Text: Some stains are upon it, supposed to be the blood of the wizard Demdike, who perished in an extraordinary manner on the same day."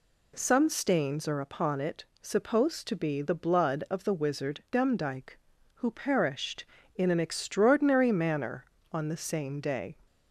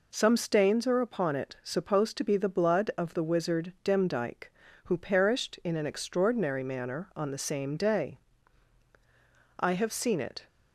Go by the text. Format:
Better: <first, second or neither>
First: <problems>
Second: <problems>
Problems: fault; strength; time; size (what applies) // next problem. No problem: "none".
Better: first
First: none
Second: goes on to say "I have seen it"; noticeable; from 9.6 s on; 0.86 s long